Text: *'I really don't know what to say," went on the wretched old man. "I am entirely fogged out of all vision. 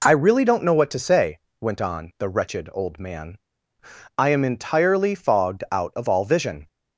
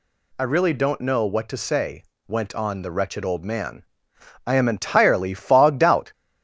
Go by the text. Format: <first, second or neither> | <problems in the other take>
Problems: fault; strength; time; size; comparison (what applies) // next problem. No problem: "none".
first | stops before "of all vision"; at 6.1 s